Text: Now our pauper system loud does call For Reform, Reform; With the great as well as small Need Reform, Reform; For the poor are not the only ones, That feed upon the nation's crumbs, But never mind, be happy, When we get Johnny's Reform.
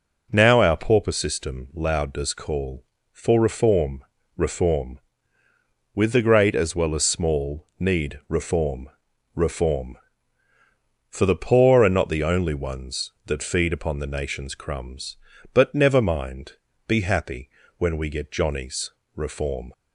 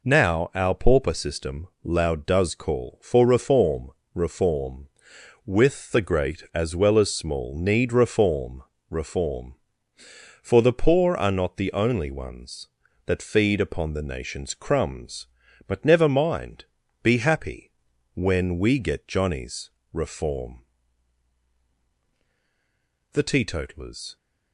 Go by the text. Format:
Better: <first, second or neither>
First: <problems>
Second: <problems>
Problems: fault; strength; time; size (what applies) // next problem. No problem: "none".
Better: first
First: pauses between "Johnny's" and "Reform"; slight; at 18.9 s; 0.26 s long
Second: pauses between "system" and "loud"; slight; at 1.6 s; 0.16 s long // pauses between "Johnny's" and "Reform"; slight; at 19.6 s; 0.22 s long // goes on to say "The teetotalers"; noticeable; from 23.1 s on; 1.0 s long